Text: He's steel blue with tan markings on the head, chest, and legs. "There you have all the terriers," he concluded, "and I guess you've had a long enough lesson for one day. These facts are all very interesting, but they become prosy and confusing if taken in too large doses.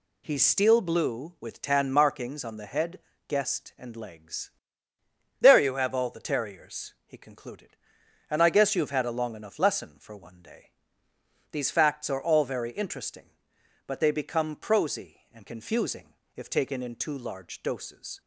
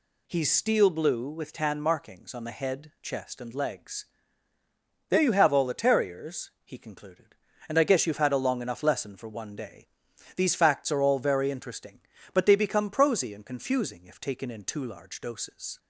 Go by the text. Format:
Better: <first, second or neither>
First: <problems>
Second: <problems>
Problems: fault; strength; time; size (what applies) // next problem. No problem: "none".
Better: second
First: says "guest" for "chest"; at 3.2 s // pauses between "confusing" and "if"; slight; at 16.1 s; 0.22 s long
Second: none